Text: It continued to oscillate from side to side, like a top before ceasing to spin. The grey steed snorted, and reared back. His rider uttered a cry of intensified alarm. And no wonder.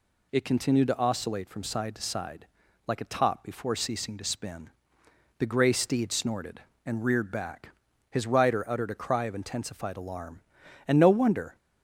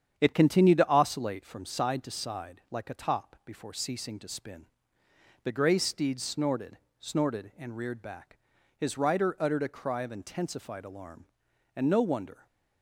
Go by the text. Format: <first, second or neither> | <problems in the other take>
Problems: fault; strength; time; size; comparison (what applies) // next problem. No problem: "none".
first | starts louder than the rest; strong; until 1.1 s; 8.5 dB // says "snorted" twice; at 6.9 s